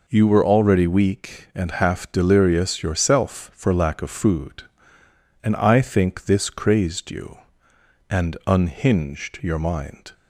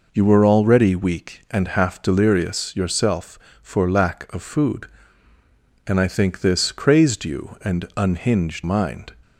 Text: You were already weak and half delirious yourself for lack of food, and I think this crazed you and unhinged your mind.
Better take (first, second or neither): first